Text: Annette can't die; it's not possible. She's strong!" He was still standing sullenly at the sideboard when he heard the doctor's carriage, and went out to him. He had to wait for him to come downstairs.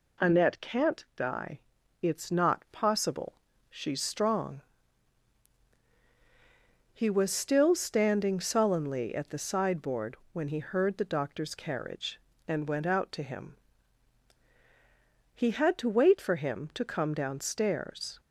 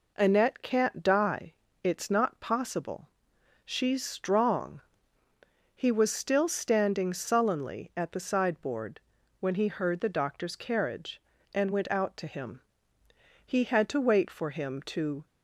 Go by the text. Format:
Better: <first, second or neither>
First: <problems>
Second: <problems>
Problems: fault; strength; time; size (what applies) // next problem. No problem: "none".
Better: first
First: pauses between "sideboard" and "when"; slight; at 10.1 s; 0.16 s long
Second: pauses between "sideboard" and "when"; at 8.9 s; 0.40 s long // stops before "come downstairs"; at 15.2 s